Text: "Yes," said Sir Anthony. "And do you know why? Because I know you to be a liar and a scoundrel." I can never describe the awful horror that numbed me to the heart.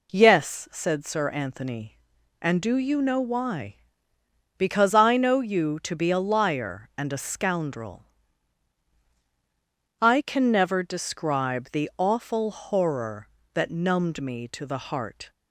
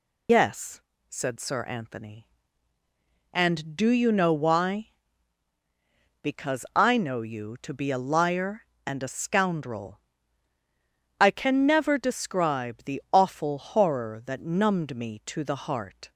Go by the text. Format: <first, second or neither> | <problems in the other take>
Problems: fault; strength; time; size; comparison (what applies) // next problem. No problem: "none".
first | loses the start of "Yes"; at 0.2 s; 125 ms